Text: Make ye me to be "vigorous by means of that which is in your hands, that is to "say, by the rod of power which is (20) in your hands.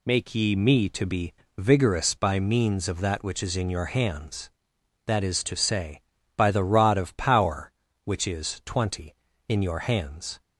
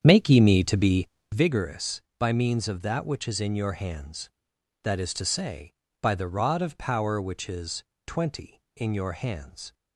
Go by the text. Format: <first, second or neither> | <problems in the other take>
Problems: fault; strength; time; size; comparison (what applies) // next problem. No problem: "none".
first | starts louder than the rest; strong; until 1.4 s; 8 dB // pauses between "be" and "vigorous"; slight; at 1.0 s; 0.24 s long; slight in the first